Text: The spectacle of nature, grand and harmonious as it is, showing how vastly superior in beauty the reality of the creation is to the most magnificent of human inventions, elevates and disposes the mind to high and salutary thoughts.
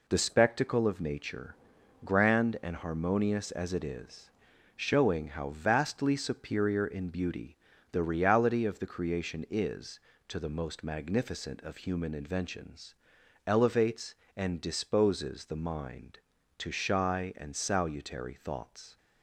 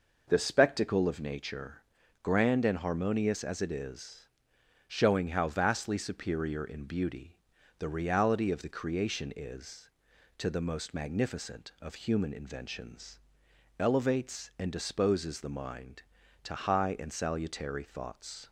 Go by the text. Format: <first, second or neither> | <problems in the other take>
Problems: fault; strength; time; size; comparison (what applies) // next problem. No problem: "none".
second | pauses between "beauty" and "the"; slight; at 7.5 s; 0.34 s long; also in the second // says "shy" for "high"; at 16.7 s